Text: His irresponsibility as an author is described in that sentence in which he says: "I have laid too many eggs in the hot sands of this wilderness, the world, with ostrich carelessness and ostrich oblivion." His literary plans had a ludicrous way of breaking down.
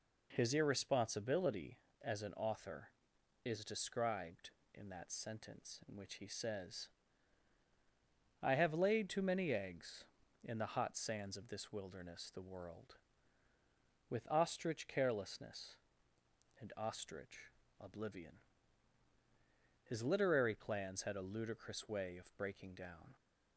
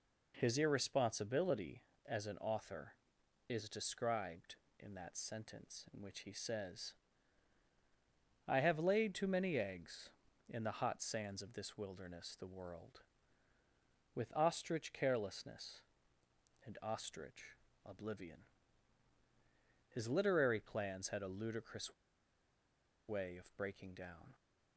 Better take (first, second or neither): first